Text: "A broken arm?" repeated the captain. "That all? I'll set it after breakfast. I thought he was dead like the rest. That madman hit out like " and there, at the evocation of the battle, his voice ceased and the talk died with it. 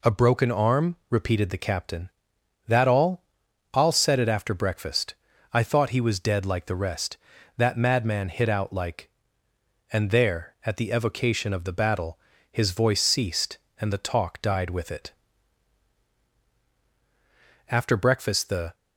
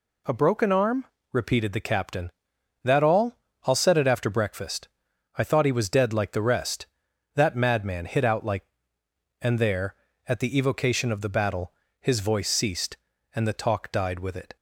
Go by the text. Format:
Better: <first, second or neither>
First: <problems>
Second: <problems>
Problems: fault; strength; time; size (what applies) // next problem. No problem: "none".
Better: second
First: goes on to say "After breakfast the"; noticeable; from 17.6 s on; 1.0 s long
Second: none